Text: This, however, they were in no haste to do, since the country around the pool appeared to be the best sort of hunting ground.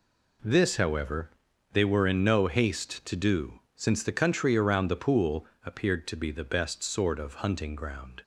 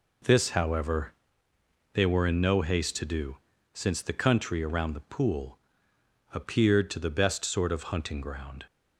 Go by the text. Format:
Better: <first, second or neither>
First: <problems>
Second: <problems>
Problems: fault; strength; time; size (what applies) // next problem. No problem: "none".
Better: first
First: pauses between "pool" and "appeared"; slight; at 5.4 s; 0.20 s long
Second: pauses between "pool" and "appeared"; noticeable; at 5.5 s; 0.76 s long // skips "be"; at 6.9 s